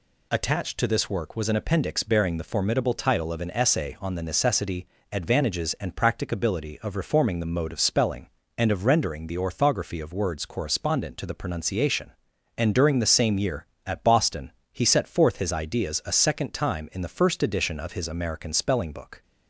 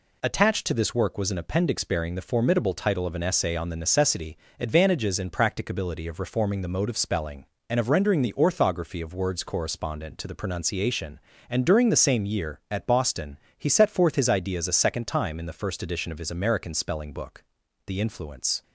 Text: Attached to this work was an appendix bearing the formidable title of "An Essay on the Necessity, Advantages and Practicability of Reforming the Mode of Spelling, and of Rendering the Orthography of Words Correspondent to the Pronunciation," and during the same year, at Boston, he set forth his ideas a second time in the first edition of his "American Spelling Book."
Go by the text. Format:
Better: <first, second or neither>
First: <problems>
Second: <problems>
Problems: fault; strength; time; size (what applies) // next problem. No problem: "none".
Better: first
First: none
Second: goes on to say "The influence"; noticeable; from 17.8 s on; 0.76 s long